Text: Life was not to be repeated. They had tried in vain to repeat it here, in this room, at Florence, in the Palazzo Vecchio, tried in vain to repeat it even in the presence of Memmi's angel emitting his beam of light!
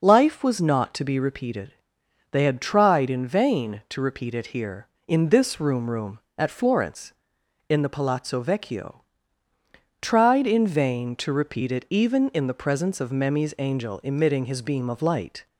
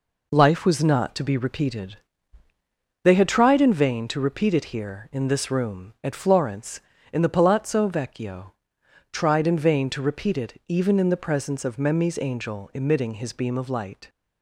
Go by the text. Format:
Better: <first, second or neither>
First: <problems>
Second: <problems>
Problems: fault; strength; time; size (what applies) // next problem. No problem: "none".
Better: second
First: says "room" twice; at 5.8 s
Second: none